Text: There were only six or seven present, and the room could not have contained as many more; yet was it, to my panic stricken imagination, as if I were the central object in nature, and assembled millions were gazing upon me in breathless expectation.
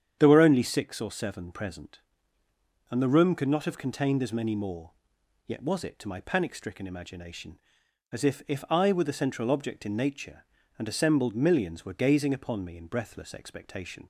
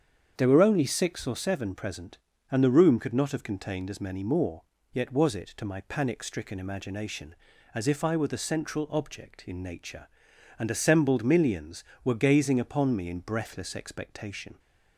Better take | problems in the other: second | starts louder than the rest; strong; until 1.2 s; 8.5 dB; strong in the second // says "if" twice; at 8.4 s

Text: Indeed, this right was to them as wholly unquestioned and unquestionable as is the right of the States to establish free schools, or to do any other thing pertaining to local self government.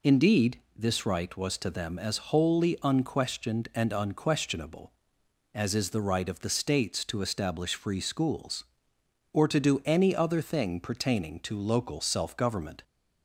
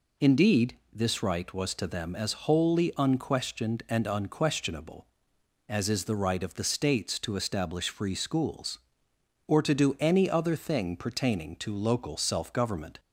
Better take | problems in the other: neither | none

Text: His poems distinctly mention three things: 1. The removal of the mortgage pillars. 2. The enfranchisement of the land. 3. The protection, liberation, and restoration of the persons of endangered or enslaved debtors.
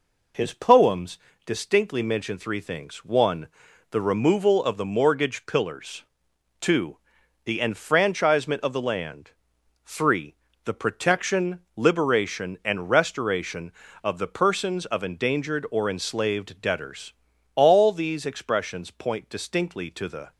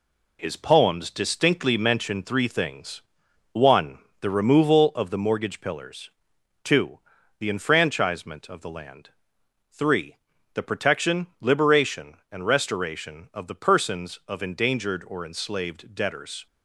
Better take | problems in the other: second | pauses between "poems" and "distinctly"; slight; at 1.1 s; 0.28 s long // goes on to say "All these expressions point distinctly to the"; strong; from 17.5 s on; 2.7 s long

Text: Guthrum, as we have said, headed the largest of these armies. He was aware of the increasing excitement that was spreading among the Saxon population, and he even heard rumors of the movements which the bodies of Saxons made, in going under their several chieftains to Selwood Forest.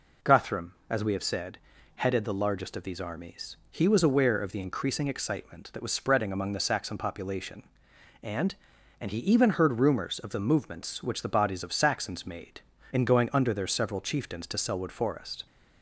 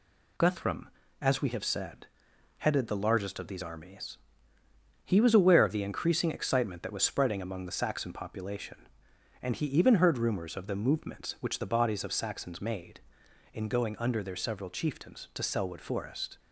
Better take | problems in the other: second | says "and" twice; at 8.9 s

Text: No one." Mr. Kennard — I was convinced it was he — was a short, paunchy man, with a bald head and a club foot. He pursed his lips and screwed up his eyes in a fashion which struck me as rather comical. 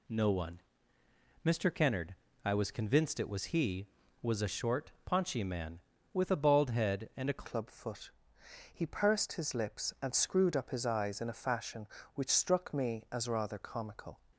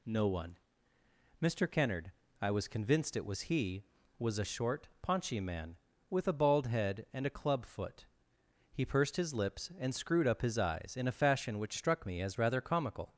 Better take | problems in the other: second | changes voice at "club"; from 7.4 s on; 6.7 s long

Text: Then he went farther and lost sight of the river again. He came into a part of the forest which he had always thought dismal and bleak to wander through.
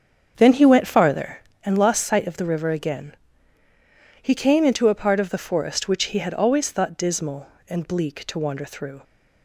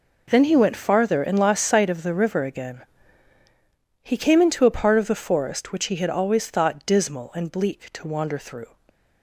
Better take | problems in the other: second | starts louder than the rest; strong; until 1.6 s; 7 dB

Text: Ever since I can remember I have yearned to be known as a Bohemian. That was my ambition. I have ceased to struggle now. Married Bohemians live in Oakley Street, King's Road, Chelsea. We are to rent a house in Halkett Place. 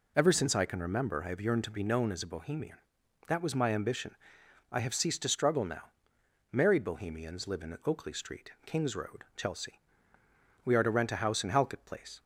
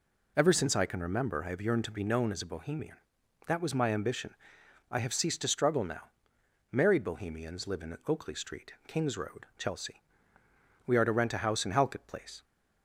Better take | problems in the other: neither | none

